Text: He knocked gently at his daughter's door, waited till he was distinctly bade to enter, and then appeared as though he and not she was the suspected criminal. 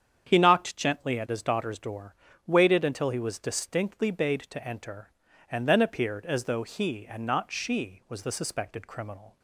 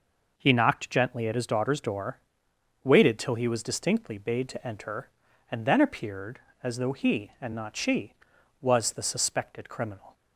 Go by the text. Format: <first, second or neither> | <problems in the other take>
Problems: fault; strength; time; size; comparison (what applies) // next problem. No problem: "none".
second | starts louder than the rest; strong; until 1.3 s; 8 dB // says "until" for "till"; at 2.8 s